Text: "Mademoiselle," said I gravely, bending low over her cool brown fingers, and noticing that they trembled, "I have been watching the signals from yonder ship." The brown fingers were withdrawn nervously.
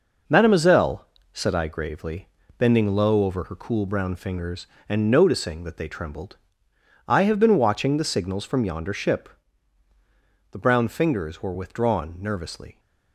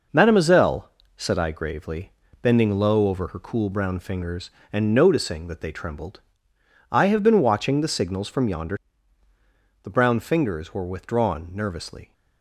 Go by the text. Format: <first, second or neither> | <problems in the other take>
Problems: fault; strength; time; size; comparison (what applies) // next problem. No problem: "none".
first | skips "ship"; at 9.2 s